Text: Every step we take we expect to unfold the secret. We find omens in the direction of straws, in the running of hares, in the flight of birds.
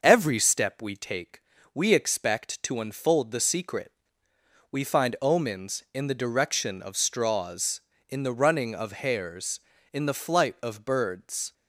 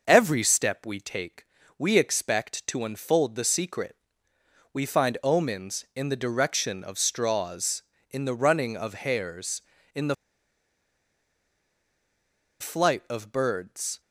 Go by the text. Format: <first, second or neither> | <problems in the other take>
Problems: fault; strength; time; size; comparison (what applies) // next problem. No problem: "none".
first | pauses between "take" and "we"; slight; at 1.4 s; 0.32 s long; slight in the first // pauses between "the" and "flight"; strong; at 10.1 s; 2.4 s long